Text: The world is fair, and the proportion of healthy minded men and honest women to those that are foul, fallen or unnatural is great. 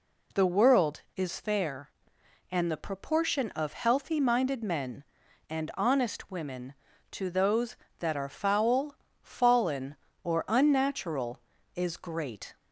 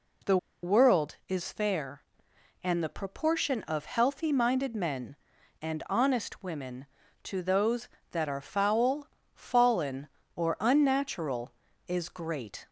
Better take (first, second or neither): first